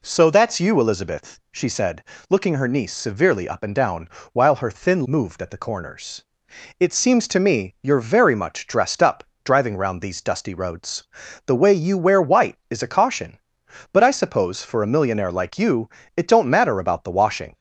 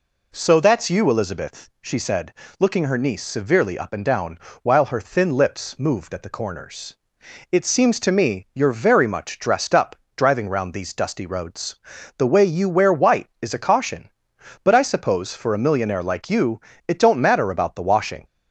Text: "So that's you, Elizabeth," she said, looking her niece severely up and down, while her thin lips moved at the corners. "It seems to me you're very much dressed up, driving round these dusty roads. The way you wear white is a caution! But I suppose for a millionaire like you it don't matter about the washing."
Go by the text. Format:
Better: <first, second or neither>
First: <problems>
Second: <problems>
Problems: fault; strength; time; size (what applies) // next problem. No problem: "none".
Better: second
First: skips "lips"; at 5.0 s // pauses between "you" and "it"; slight; at 15.8 s; 0.26 s long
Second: pauses between "you" and "it"; slight; at 16.6 s; 0.26 s long